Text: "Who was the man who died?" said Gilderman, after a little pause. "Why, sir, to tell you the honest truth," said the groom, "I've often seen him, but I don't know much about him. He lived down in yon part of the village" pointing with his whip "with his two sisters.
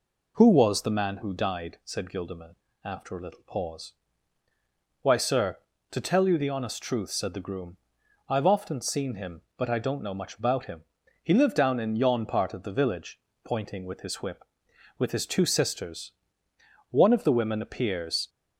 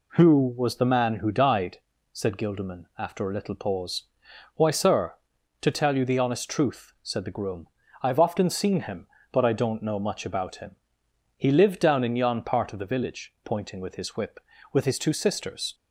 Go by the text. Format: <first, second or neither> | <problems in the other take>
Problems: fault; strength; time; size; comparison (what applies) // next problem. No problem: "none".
second | pauses between "village" and "pointing"; slight; at 13.2 s; 0.22 s long // goes on to say "One of the women appears"; from 16.8 s on; 1.4 s long